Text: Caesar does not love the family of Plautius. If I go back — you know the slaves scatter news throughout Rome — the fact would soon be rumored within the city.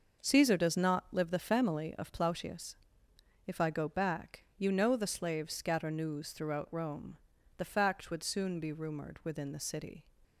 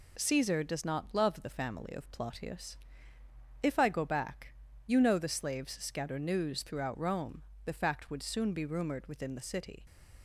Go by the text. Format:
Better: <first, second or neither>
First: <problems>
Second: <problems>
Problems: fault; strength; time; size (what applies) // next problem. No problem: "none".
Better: second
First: starts louder than the rest; noticeable; until 1.3 s; 6 dB // says "live" for "love"; at 1.1 s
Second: none